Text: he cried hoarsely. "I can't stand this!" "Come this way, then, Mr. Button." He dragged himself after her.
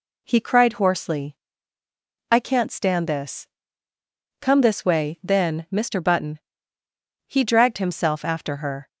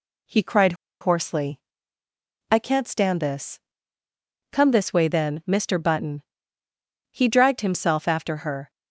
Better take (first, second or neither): first